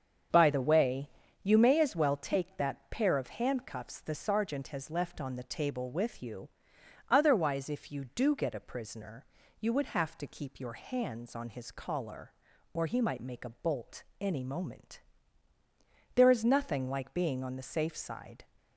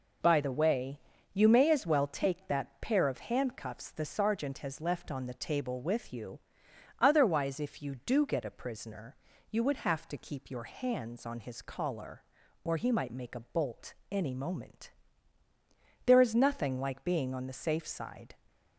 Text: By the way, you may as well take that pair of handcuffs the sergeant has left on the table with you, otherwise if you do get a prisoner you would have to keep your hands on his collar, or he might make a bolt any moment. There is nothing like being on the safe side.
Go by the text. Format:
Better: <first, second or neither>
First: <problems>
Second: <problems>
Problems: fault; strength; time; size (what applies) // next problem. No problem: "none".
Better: second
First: starts louder than the rest; strong; until 1.3 s; 7.5 dB // pauses between "prisoner" and "you"; slight; at 9.2 s; 0.34 s long // pauses between "bolt" and "any"; slight; at 14.0 s; 0.18 s long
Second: pauses between "prisoner" and "you"; slight; at 9.1 s; 0.34 s long // pauses between "bolt" and "any"; slight; at 13.9 s; 0.18 s long